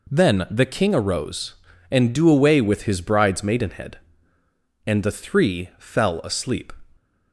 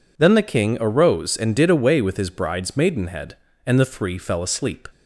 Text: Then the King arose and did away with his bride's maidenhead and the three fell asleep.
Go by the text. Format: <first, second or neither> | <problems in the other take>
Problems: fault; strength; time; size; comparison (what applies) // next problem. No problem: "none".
second | says "do" for "did"; at 2.1 s